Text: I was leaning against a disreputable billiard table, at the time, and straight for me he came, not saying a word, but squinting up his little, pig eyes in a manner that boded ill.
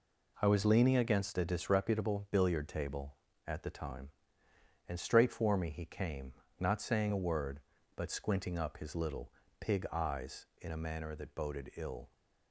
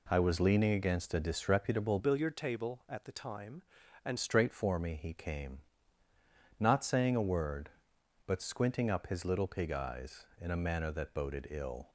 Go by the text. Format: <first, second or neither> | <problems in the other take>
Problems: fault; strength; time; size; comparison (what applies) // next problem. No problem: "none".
first | changes voice from "billiard" to "and"; from 1.9 to 4.1 s; 2.2 s long